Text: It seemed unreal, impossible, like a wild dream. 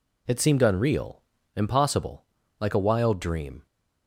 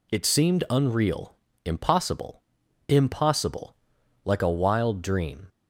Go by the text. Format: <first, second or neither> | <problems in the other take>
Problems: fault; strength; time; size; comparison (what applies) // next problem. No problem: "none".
first | says "impossible" twice; at 2.9 s